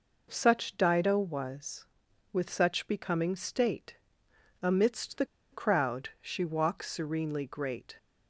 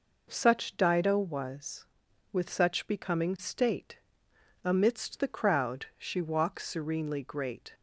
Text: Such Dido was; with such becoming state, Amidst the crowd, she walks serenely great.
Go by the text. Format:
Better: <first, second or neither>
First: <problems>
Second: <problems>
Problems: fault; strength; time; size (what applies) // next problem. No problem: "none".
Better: second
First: pauses between "the" and "crowd"; slight; at 5.2 s; 0.27 s long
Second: none